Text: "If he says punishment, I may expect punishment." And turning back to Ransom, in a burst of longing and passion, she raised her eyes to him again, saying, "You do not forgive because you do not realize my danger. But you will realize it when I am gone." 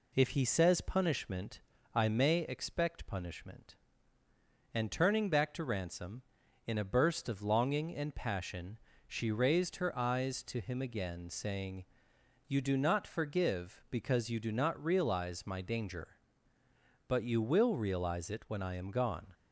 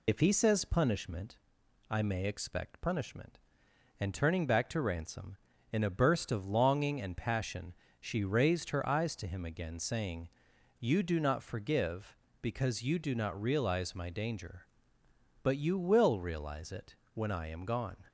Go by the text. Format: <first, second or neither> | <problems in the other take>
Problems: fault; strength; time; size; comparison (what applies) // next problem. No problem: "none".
first | loses the start of "If"; at 0.0 s; 45 ms // pauses between "it" and "when"; slight; at 16.9 s; 0.18 s long